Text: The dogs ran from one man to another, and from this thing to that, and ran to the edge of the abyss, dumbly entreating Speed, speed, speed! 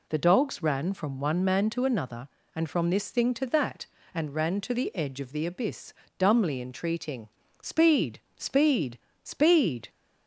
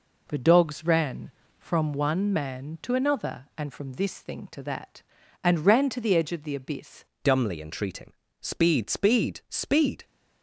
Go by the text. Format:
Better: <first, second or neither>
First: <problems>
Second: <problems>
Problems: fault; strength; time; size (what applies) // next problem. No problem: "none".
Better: first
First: pauses between "entreating" and "Speed"; slight; at 7.2 s; 0.32 s long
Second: changes voice at "dumbly"; from 7.2 s on; 2.8 s long // pauses between "entreating" and "Speed"; slight; at 8.1 s; 0.28 s long